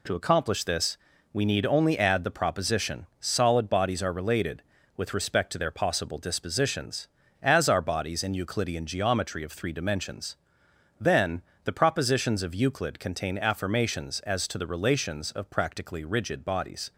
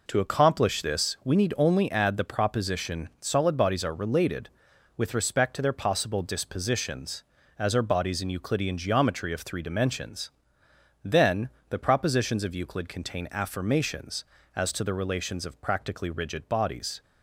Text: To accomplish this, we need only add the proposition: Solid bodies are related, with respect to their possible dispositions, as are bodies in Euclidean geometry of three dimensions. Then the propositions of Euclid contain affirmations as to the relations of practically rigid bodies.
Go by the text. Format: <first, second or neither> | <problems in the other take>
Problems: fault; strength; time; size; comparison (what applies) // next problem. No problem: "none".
neither | pauses between "Then" and "the"; slight; the same in both